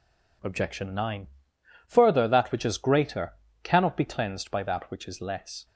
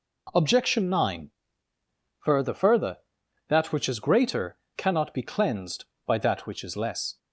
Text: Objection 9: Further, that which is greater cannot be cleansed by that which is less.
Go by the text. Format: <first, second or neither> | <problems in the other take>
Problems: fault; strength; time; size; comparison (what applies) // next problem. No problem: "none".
first | says "Further" twice; at 2.5 s // pauses between "greater" and "cannot"; slight; at 4.5 s; 0.18 s long; slight in the first